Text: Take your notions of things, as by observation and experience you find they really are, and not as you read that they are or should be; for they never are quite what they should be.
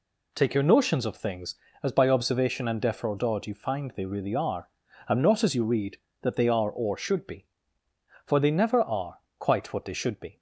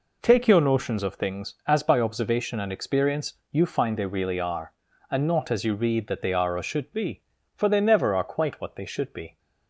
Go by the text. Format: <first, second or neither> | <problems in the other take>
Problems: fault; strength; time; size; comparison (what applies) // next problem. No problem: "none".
second | says "defraudod" for "experience"; at 2.8 s // pauses between "are" and "quite"; slight; at 9.1 s; 0.20 s long